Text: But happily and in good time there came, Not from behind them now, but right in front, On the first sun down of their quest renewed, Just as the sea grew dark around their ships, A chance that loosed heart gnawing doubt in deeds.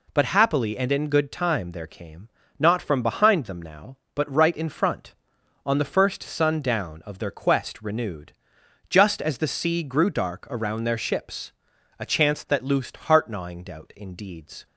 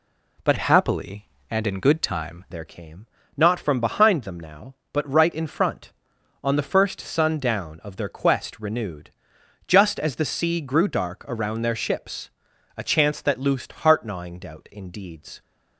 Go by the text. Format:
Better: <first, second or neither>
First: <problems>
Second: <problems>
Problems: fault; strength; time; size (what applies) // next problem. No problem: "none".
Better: first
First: none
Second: changes voice from "happily" to "time"; from 0.5 to 2.4 s; 1.9 s long